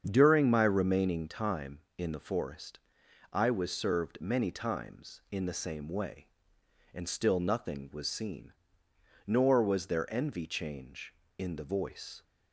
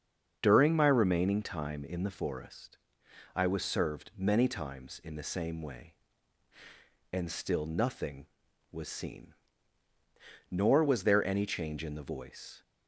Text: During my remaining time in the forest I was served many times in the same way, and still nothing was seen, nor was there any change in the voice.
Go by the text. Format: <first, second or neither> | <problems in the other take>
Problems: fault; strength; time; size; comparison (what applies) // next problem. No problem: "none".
second | starts louder than the rest; strong; until 1.0 s; 7.5 dB; also in the second // pauses between "forest" and "I"; noticeable; at 2.7 s; 0.56 s long; noticeable in the second // says "envy" for "any"; at 10.1 s